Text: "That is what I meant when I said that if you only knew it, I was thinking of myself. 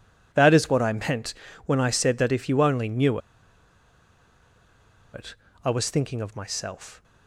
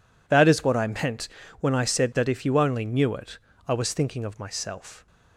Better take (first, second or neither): second